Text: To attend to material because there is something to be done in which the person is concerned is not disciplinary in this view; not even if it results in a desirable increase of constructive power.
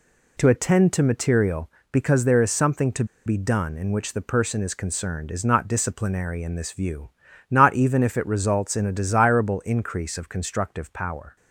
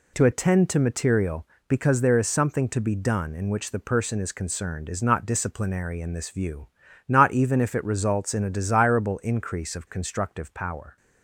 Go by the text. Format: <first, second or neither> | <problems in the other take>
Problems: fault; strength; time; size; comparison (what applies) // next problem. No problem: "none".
second | pauses between "to" and "be"; slight; at 3.0 s; 0.21 s long